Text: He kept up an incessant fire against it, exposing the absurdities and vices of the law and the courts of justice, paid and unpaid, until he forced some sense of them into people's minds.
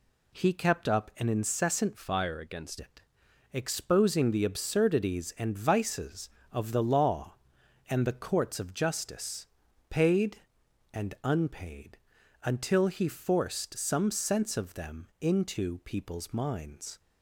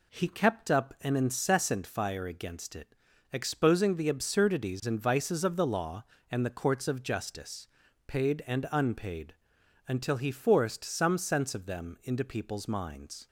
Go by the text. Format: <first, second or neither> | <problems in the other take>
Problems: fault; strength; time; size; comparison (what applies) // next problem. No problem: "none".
second | changes voice from "fire" to "against"; from 1.9 to 2.7 s; 0.8 s long